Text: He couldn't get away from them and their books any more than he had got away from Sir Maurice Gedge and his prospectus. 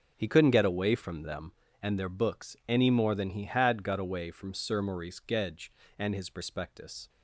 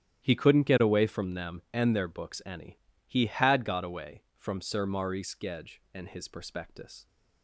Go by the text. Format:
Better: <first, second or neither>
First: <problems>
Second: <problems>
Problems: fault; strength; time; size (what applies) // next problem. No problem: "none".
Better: first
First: none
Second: starts louder than the rest; strong; until 1.2 s; 11 dB // skips "more than"; at 2.9 s